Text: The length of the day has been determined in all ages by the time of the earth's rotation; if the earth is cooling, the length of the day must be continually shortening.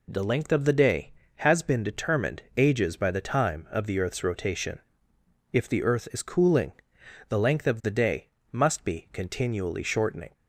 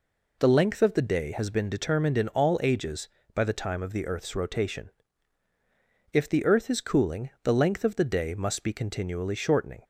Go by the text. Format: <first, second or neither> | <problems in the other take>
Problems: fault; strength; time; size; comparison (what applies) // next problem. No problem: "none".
second | skips "in all"; at 2.4 s // pauses between "day" and "must"; slight; at 8.2 s; 0.24 s long